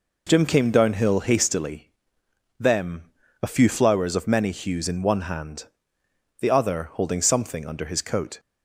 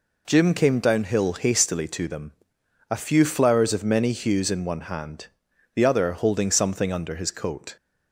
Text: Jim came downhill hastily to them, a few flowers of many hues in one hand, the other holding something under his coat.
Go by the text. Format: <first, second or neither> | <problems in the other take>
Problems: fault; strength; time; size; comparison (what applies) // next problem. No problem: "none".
second | skips "to"; at 2.2 s